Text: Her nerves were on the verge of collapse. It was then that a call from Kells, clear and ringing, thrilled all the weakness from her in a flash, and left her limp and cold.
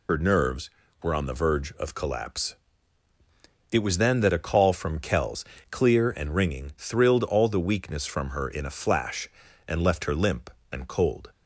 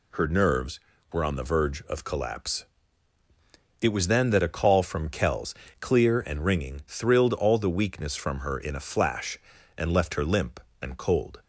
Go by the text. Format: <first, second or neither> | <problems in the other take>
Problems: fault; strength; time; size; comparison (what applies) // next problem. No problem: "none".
second | loses the start of "Her"; at 0.0 s; 75 ms